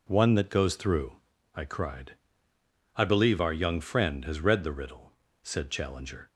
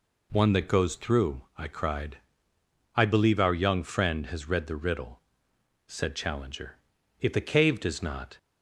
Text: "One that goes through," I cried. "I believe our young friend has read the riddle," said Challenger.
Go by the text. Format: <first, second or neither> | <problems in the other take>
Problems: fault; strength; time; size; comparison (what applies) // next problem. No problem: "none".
first | goes on to say "If the cave does not"; noticeable; from 7.1 s on; 1.1 s long